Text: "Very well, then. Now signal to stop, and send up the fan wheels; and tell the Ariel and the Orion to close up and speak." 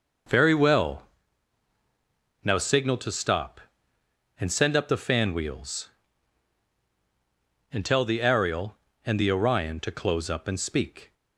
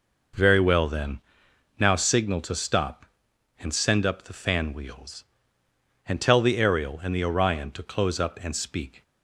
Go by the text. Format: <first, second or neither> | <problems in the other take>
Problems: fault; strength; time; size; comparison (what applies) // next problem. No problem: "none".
second | skips "then"; at 1.7 s